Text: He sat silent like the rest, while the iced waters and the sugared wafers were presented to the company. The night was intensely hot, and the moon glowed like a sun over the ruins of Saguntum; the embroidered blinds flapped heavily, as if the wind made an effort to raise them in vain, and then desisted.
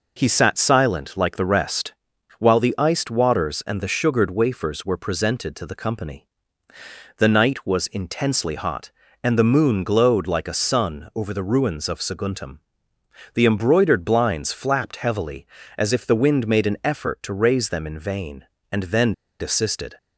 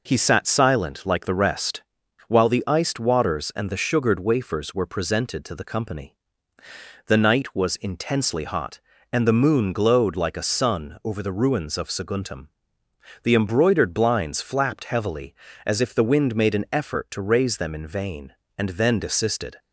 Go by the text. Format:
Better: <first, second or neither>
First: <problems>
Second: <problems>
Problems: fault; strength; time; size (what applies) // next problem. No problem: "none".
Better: second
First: pauses between "then" and "desisted"; slight; at 19.1 s; 0.26 s long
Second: none